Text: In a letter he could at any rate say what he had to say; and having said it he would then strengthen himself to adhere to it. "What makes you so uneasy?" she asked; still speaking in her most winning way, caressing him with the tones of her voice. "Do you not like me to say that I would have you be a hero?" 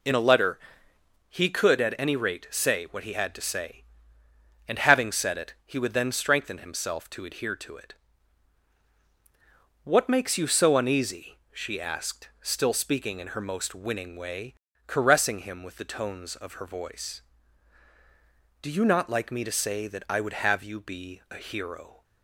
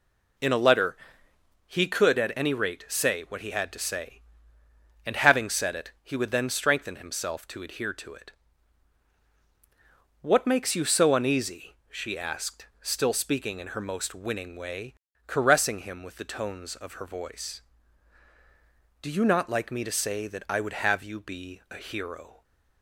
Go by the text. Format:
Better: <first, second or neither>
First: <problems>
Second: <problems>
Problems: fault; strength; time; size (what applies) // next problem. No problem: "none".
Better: neither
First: pauses between "letter" and "he"; noticeable; at 0.5 s; 0.74 s long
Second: pauses between "letter" and "he"; noticeable; at 0.9 s; 0.74 s long